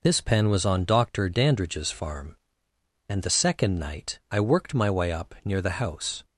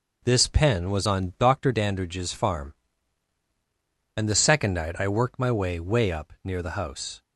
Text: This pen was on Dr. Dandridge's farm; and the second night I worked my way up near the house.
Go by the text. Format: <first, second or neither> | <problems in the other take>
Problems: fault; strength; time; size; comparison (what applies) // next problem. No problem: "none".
first | says "way" twice; at 5.7 s